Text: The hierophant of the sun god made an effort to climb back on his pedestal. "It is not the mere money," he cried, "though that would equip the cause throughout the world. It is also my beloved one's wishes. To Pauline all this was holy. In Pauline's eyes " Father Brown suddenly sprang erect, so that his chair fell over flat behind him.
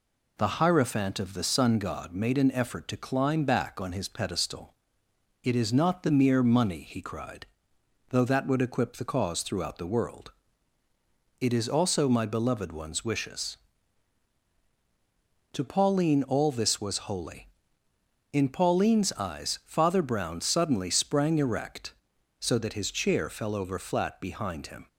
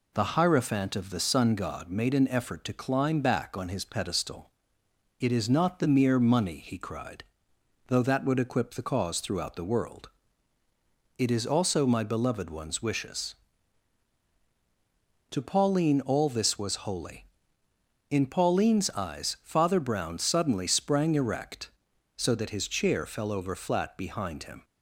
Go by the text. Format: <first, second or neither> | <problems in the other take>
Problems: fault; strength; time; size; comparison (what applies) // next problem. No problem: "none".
neither | none